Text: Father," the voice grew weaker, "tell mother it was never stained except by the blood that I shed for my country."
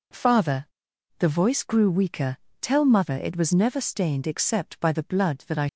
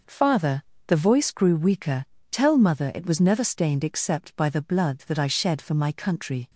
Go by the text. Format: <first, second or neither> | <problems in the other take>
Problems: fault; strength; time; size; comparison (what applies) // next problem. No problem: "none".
second | stops before "shed for my country"; at 5.6 s